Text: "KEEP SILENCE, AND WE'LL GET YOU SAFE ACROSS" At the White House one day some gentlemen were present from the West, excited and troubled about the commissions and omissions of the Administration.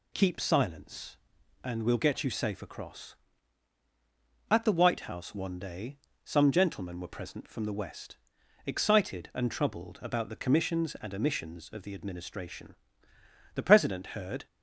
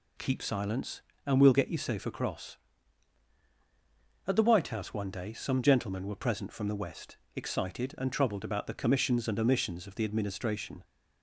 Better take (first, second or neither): second